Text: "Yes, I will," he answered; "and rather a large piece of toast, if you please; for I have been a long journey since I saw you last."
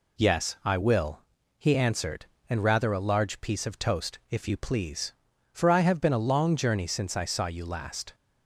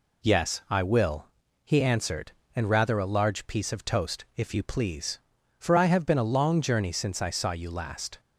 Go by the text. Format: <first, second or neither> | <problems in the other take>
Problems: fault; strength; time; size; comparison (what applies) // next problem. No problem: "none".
neither | none